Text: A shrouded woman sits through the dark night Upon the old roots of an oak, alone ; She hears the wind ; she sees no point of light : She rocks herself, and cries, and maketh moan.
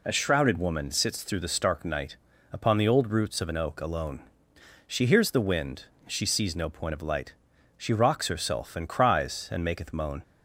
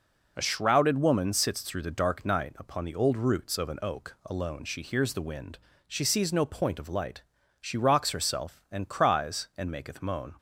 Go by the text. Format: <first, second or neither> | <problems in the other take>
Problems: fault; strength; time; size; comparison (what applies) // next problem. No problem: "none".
second | says "stark" for "dark"; at 1.4 s // pauses between "night" and "Upon"; at 2.1 s; 0.36 s long